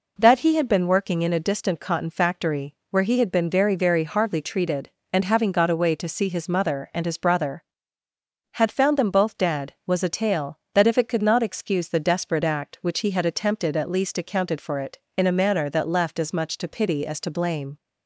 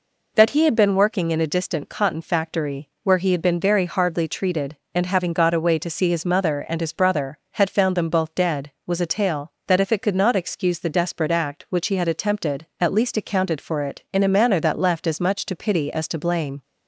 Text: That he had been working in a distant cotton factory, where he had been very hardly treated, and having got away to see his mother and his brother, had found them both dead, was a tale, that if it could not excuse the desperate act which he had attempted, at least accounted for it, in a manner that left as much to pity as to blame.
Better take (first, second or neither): second